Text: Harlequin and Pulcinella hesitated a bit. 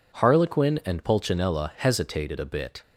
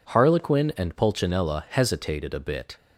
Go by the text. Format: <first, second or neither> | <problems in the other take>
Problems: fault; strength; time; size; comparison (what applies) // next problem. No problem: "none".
neither | none